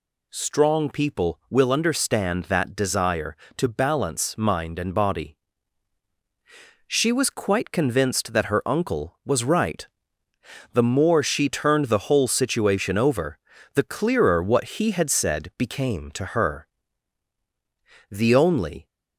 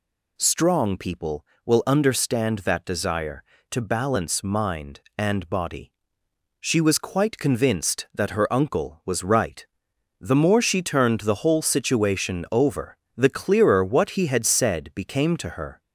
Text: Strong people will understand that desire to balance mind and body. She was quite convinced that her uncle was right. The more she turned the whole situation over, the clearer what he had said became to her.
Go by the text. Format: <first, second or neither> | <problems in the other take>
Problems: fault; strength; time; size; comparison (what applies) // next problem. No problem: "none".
second | goes on to say "The only"; noticeable; from 18.1 s on; 0.76 s long